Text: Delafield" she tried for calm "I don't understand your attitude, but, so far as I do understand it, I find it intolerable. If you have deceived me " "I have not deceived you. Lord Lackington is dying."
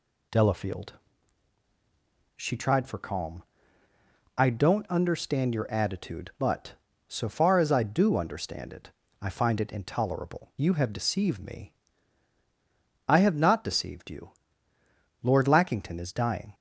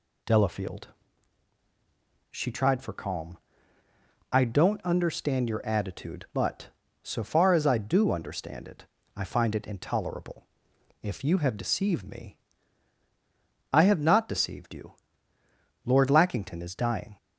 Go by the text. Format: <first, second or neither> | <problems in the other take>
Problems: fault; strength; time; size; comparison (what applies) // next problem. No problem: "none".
second | pauses between "Delafield" and "she"; strong; at 0.9 s; 1.4 s long; strong in the second // pauses between "calm" and "I"; noticeable; at 3.4 s; 0.96 s long; noticeable in the second // skips "If"; at 10.5 s